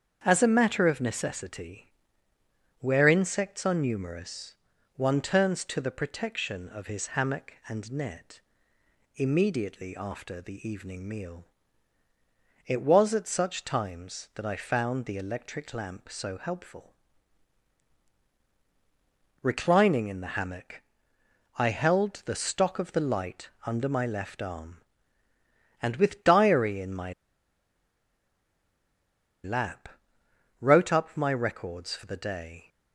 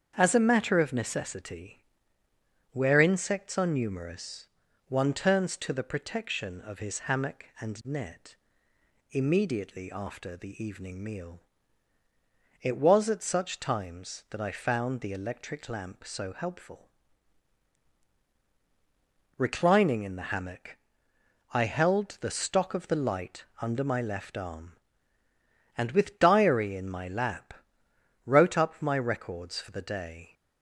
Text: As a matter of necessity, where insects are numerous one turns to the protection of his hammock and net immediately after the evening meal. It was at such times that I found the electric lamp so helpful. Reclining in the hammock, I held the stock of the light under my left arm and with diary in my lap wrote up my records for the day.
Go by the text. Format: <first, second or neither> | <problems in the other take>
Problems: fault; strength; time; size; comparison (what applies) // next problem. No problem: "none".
second | starts louder than the rest; strong; until 1.2 s; 7.5 dB; strong in the second // pauses between "numerous" and "one"; at 4.5 s; 0.40 s long; also in the second // pauses between "net" and "immediately"; noticeable; at 8.3 s; 0.78 s long; noticeable in the second // pauses between "light" and "under"; slight; at 23.4 s; 0.18 s long; slight in the second // pauses between "my" and "lap"; strong; at 27.1 s; 2.3 s long // pauses between "lap" and "wrote"; noticeable; at 29.8 s; 0.72 s long; noticeable in the second